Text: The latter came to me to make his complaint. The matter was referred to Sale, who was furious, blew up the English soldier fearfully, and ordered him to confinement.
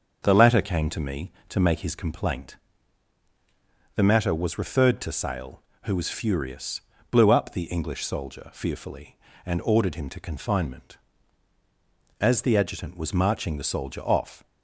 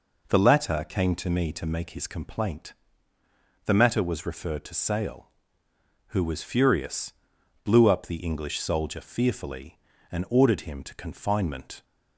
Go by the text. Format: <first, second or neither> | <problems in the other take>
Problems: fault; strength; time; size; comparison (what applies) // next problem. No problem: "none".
second | starts louder than the rest; until 1.2 s; 6.5 dB // goes on to say "As the Adjutant was marching the soldier off"; strong; from 12.2 s on; 2.2 s long